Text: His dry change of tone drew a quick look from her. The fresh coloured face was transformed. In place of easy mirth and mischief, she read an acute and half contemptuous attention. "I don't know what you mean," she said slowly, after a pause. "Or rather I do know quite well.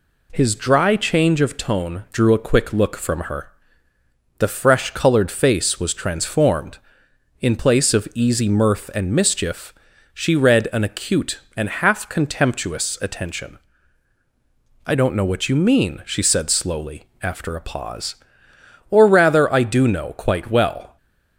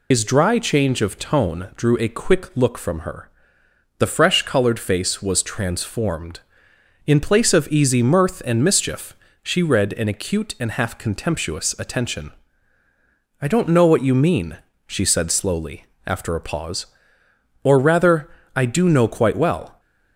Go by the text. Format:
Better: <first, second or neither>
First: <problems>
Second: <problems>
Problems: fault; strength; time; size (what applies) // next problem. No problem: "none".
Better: first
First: none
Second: loses the start of "His"; at 0.1 s; 110 ms // pauses between "rather" and "I"; slight; at 18.2 s; 0.26 s long